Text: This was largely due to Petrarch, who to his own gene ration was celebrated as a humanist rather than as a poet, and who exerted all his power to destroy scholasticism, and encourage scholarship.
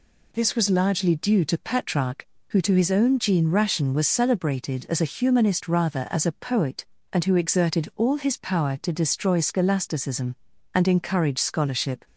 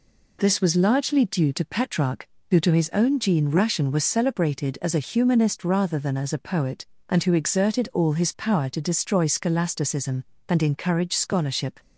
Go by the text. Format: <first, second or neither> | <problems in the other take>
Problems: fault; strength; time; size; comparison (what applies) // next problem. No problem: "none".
second | skips "than"; at 6.0 s